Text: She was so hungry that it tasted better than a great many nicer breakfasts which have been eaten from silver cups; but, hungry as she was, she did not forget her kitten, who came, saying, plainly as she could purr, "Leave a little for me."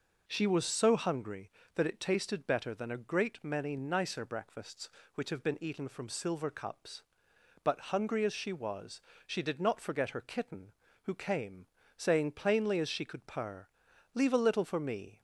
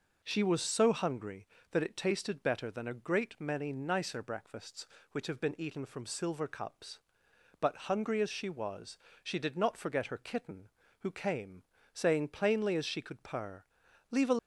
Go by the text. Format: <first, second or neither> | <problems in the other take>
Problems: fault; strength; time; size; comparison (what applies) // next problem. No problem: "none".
first | stops before "little for me"; at 14.3 s